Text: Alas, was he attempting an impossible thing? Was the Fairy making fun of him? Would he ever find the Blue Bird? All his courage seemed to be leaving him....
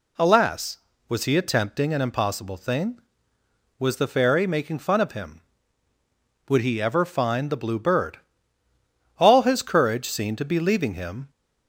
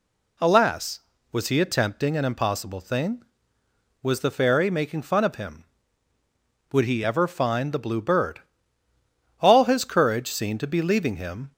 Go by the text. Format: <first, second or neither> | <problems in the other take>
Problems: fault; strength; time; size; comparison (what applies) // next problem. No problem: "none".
neither | none